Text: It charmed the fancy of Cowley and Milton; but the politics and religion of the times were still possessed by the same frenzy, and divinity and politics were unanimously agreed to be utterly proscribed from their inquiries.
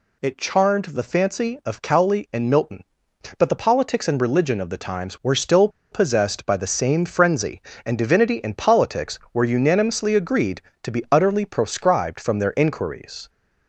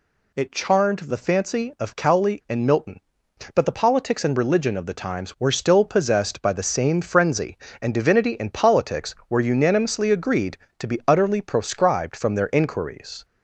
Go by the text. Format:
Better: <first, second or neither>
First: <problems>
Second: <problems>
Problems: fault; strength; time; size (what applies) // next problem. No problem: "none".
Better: second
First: pauses between "still" and "possessed"; slight; at 5.6 s; 0.23 s long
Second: none